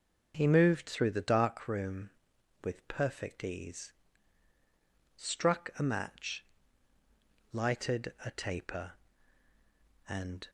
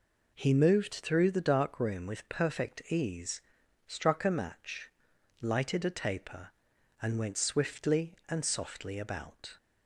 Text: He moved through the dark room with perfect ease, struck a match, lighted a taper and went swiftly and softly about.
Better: second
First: stops before "went swiftly and softly about"; at 10.4 s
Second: none

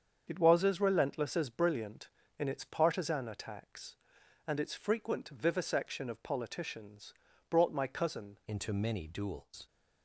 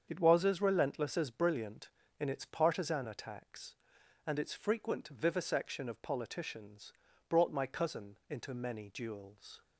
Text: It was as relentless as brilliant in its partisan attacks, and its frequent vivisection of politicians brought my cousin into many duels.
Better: second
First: starts louder than the rest; strong; until 1.2 s; 7 dB // pauses between "politicians" and "brought"; slight; at 7.1 s; 0.36 s long // changes voice at "into"; from 8.4 s on; 1.2 s long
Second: starts louder than the rest; strong; until 1.1 s; 7 dB // pauses between "politicians" and "brought"; slight; at 6.9 s; 0.36 s long

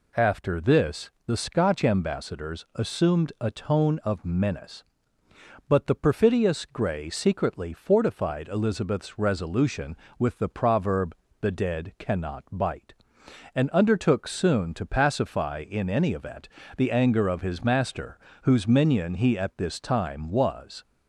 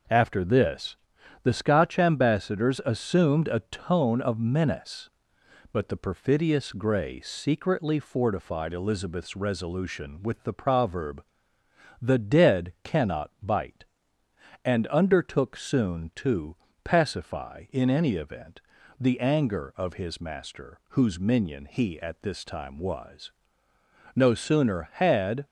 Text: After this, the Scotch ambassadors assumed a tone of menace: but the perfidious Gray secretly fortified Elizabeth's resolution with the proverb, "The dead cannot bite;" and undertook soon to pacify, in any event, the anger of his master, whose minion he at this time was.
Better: first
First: none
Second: pauses between "to" and "pacify"; slight; at 16.5 s; 0.28 s long // goes on to say "No sooner had"; noticeable; from 24.1 s on; 1.2 s long

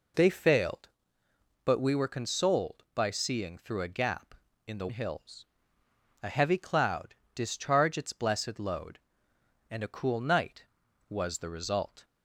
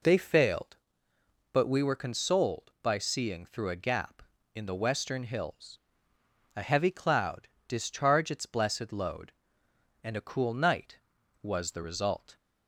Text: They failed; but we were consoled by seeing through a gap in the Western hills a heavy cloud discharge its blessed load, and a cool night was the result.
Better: second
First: skips "Western"; at 4.8 s // pauses between "hills" and "a"; noticeable; at 5.4 s; 0.78 s long // pauses between "cloud" and "discharge"; slight; at 7.1 s; 0.22 s long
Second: pauses between "hills" and "a"; noticeable; at 5.7 s; 0.78 s long // pauses between "cloud" and "discharge"; slight; at 7.4 s; 0.22 s long

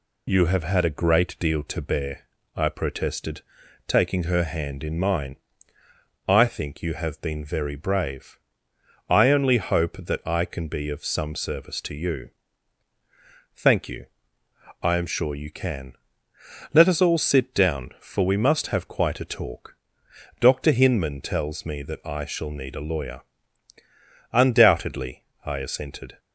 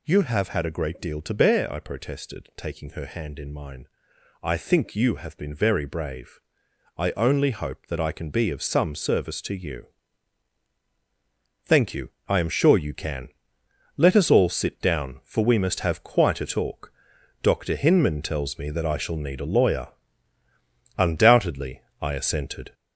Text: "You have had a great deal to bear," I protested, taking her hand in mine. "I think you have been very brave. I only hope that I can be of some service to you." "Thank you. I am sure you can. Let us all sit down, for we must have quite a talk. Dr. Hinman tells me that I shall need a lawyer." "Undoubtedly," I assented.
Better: first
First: none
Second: gets louder; noticeable; throughout; 4.5 dB

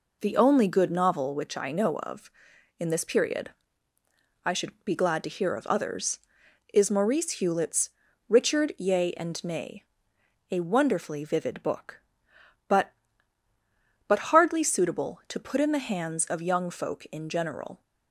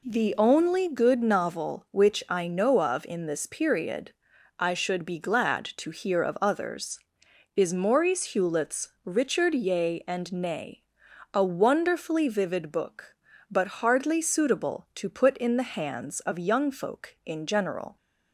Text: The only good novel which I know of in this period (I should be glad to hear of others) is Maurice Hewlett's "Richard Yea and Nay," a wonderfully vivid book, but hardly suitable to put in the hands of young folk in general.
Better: second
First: pauses between "Hewlett's" and "Richard"; slight; at 7.9 s; 0.36 s long // says "but" twice; at 14.0 s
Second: pauses between "Hewlett's" and "Richard"; slight; at 8.8 s; 0.16 s long

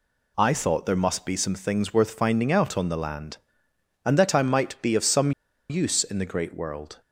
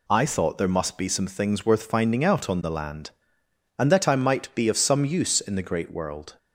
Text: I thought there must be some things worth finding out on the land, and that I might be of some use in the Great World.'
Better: second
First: pauses between "some" and "use"; at 5.3 s; 0.39 s long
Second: none

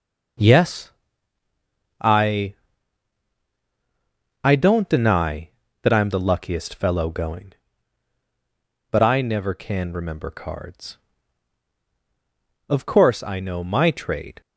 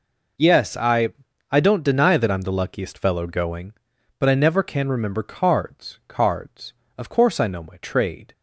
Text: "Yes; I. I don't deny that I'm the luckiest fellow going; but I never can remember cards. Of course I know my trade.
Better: first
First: none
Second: says "cards" twice; at 6.0 s

